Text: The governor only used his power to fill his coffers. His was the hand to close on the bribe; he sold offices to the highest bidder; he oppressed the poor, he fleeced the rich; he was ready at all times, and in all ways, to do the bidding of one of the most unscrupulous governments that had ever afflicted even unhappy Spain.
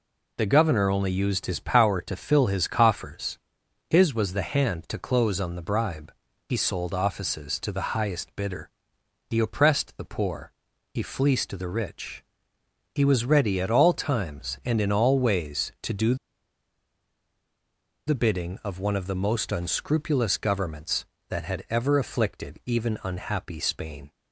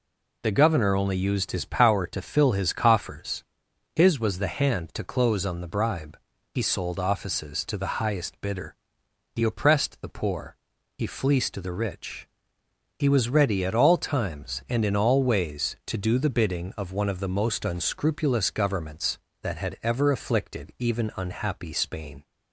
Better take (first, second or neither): second